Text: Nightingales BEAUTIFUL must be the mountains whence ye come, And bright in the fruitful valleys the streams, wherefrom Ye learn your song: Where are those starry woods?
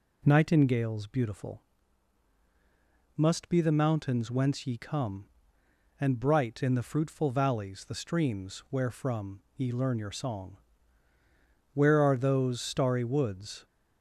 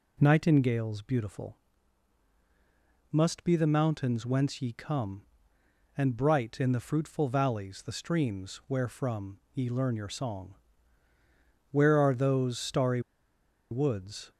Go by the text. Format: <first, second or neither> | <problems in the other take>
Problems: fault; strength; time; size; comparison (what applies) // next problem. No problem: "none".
first | pauses between "BEAUTIFUL" and "must"; strong; at 1.5 s; 1.5 s long; strong in the first // pauses between "wherefrom" and "Ye"; slight; at 9.3 s; 0.16 s long; slight in the first // pauses between "starry" and "woods"; noticeable; at 13.0 s; 0.70 s long